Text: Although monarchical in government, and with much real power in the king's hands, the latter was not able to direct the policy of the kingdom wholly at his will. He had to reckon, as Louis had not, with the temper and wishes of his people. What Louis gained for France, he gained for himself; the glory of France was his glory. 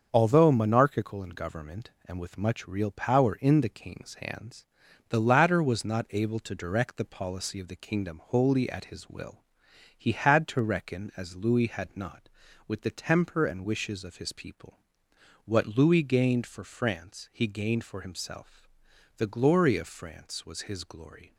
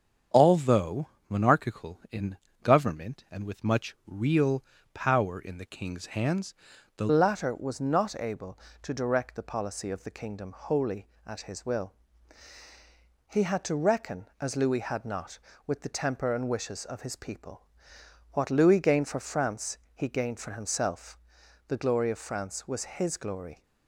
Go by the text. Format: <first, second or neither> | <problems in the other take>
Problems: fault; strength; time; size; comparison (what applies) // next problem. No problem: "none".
first | starts louder than the rest; strong; until 1.5 s; 7.5 dB; also in the first // pauses between "Although" and "monarchical"; slight; at 1.0 s; 0.20 s long // pauses between "in" and "government"; slight; at 2.3 s; 0.26 s long // pauses between "real" and "power"; slight; at 4.6 s; 0.30 s long // changes voice at "latter"; from 7.1 s on; 16.5 s long